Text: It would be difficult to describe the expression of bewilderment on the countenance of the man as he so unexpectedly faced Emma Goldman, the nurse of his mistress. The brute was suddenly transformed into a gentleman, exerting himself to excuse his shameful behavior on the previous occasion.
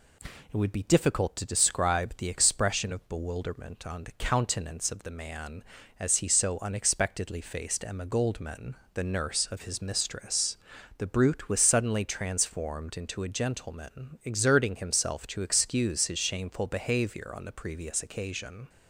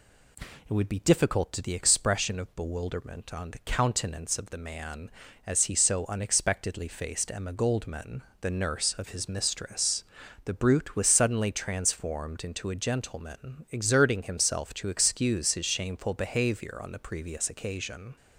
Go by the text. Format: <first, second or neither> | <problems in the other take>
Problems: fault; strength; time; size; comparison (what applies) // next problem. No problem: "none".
first | skips "describe"; at 1.6 s